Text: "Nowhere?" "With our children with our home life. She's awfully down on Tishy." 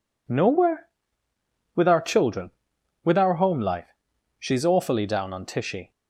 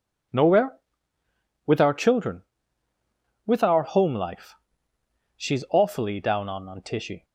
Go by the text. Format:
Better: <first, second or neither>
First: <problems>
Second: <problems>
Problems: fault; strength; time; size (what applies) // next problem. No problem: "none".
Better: first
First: none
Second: says "on" twice; at 6.6 s